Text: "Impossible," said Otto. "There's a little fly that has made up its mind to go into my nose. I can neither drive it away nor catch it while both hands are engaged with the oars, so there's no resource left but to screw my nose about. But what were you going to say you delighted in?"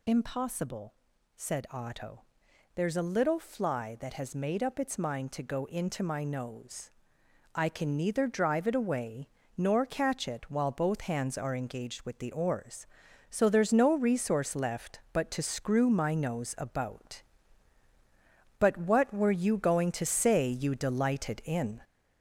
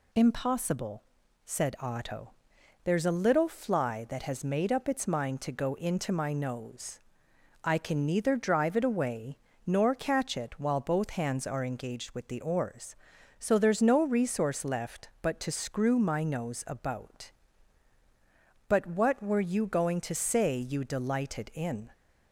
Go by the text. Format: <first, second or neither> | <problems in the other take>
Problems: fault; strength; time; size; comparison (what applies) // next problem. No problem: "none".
second | gets louder; noticeable; throughout; 4.5 dB // pauses between "away" and "nor"; slight; at 9.2 s; 0.28 s long; slight in the second